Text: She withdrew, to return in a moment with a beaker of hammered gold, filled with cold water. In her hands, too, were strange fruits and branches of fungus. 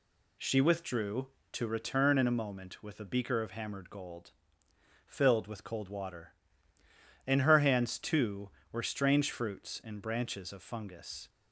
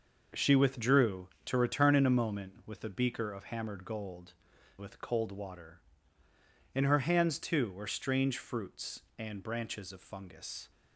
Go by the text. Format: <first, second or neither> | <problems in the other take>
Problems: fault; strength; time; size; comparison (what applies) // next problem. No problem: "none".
first | skips "filled"; at 4.5 s